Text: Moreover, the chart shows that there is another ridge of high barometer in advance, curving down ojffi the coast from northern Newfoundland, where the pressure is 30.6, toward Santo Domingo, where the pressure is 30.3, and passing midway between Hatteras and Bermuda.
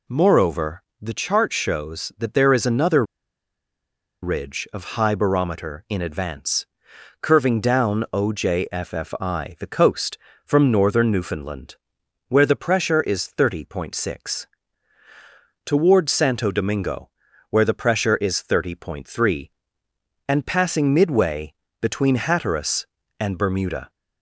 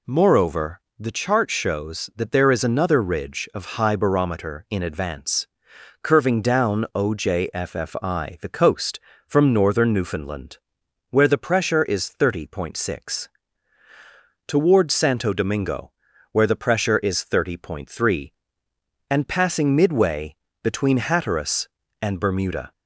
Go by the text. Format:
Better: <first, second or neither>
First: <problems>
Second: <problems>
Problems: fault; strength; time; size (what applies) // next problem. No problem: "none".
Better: second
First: pauses between "another" and "ridge"; at 3.0 s; 1.1 s long // pauses between "midway" and "between"; slight; at 21.5 s; 0.26 s long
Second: pauses between "midway" and "between"; slight; at 20.3 s; 0.26 s long